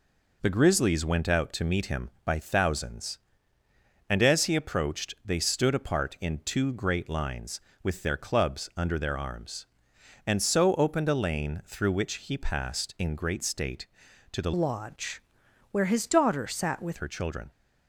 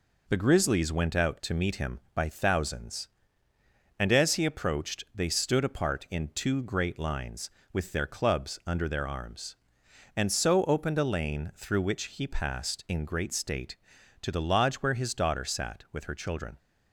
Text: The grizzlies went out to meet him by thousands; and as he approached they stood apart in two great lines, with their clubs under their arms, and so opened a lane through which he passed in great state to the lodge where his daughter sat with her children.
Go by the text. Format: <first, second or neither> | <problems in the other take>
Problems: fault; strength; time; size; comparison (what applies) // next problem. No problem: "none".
second | changes voice from "lodge" to "with"; from 14.5 to 16.9 s; 2.4 s long // pauses between "lodge" and "where"; noticeable; at 15.2 s; 0.48 s long